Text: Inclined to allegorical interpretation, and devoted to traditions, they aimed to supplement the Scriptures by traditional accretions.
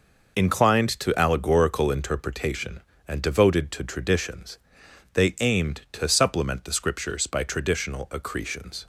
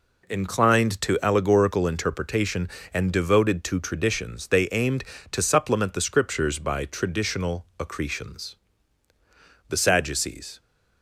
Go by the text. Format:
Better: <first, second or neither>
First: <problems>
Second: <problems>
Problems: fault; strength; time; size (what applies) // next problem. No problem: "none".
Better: first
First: none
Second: goes on to say "The Sadducees"; noticeable; from 9.6 s on; 0.92 s long